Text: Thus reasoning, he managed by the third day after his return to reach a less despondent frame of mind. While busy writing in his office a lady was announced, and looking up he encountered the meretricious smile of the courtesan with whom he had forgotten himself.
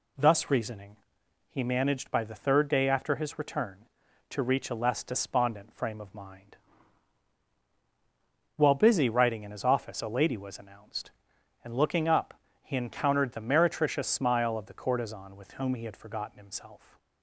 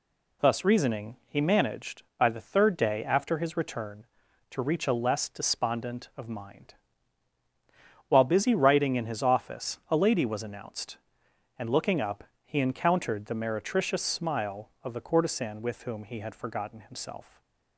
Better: first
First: pauses between "up" and "he"; slight; at 12.3 s; 0.28 s long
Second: skips "frame"; at 6.1 s // pauses between "up" and "he"; slight; at 12.2 s; 0.22 s long // stays silent after the last word; slight; from 17.2 s on; 0.5 s long

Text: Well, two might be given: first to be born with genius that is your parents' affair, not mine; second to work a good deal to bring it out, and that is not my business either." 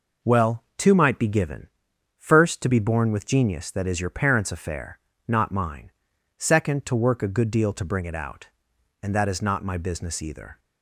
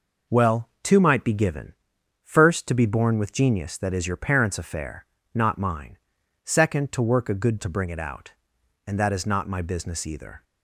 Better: first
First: none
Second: skips "deal"; at 7.5 s

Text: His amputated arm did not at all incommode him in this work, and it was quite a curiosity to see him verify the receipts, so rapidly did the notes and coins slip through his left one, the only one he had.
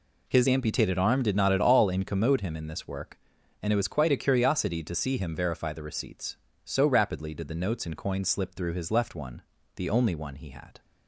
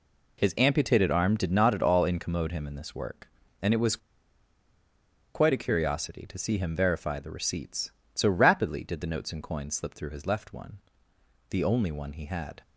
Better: first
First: none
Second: pauses between "was" and "quite"; strong; at 3.9 s; 1.3 s long

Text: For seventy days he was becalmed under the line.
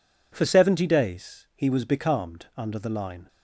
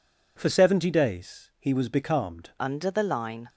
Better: first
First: none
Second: changes voice at "under"; from 2.5 s on; 0.9 s long

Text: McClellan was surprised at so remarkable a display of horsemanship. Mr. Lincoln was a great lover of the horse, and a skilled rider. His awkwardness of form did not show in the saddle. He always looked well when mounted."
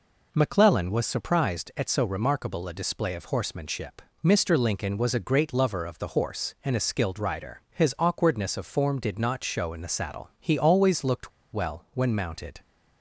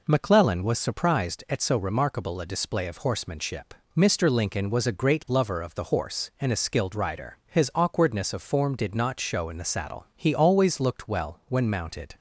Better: second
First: pauses between "looked" and "well"; slight; at 11.3 s; 0.22 s long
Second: none

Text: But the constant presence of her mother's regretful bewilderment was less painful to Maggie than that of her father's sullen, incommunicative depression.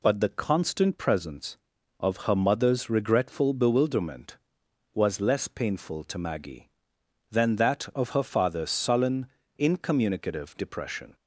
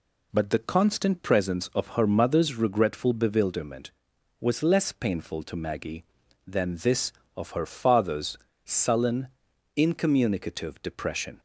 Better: first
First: none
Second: says "this" for "that"; at 6.7 s // pauses between "father's" and "sullen"; slight; at 8.3 s; 0.26 s long

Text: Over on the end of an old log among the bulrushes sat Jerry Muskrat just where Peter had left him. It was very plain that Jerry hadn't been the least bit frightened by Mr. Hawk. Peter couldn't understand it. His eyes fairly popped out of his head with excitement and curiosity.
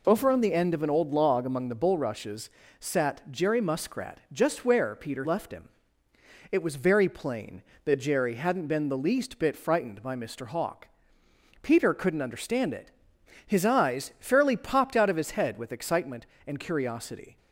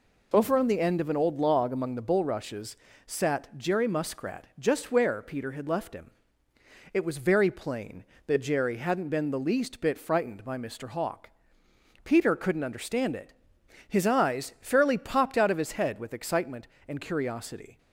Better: second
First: pauses between "bulrushes" and "sat"; slight; at 2.4 s; 0.28 s long // skips "had"; at 5.2 s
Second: pauses between "bulrushes" and "sat"; slight; at 2.7 s; 0.28 s long

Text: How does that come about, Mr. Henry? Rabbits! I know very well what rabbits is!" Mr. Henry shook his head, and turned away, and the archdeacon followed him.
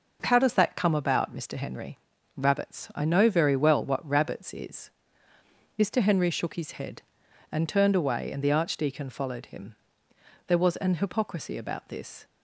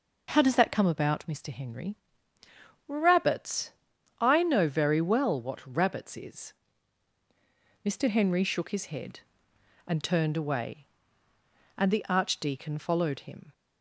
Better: second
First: goes on to say "There was an hypocrisy about this"; strong; from 10.4 s on; 1.7 s long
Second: none

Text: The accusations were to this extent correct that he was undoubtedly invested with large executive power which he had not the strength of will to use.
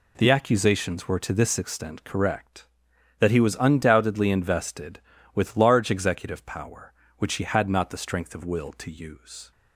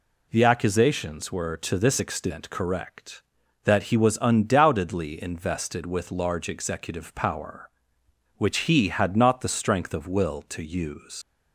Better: first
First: none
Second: leaves "use" unfinished; at 11.2 s; 105 ms

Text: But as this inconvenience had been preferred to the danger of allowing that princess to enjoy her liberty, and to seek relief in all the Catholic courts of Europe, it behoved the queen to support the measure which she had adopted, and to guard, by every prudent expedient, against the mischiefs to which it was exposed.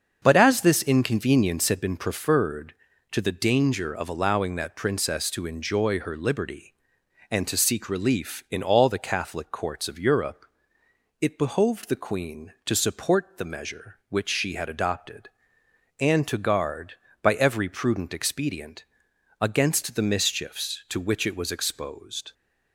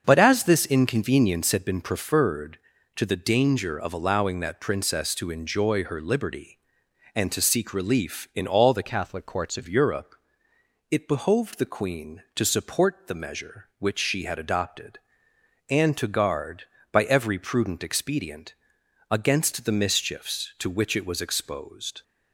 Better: first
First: starts louder than the rest; until 1.2 s; 6.5 dB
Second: starts louder than the rest; until 1.0 s; 7 dB // changes voice from "Catholic" to "of"; from 8.8 to 9.6 s; 0.8 s long

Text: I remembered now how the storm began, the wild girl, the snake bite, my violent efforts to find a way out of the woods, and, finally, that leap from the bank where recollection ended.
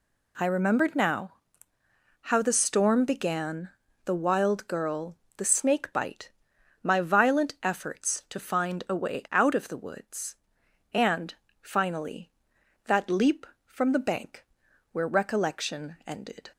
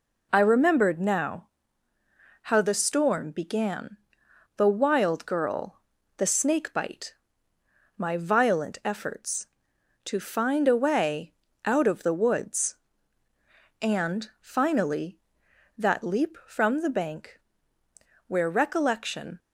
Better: first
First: pauses between "now" and "how"; noticeable; at 1.3 s; 0.90 s long // pauses between "bank" and "where"; noticeable; at 14.4 s; 0.48 s long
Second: pauses between "now" and "how"; noticeable; at 1.4 s; 0.96 s long // pauses between "way" and "out"; slight; at 11.3 s; 0.32 s long // pauses between "bank" and "where"; noticeable; at 17.3 s; 0.87 s long // stops before "ended"; at 19.3 s

